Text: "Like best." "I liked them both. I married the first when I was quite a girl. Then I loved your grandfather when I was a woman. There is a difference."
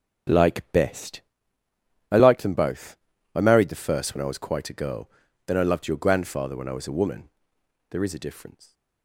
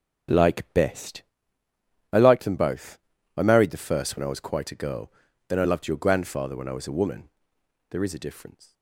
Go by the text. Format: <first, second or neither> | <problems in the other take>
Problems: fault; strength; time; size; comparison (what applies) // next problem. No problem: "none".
neither | none